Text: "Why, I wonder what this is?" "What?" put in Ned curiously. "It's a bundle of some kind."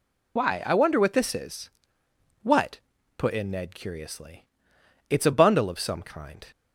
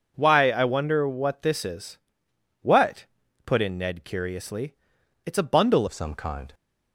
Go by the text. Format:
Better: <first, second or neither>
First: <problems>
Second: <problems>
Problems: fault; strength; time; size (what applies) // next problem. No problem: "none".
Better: first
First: none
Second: changes voice at "of"; from 5.8 s on; 0.7 s long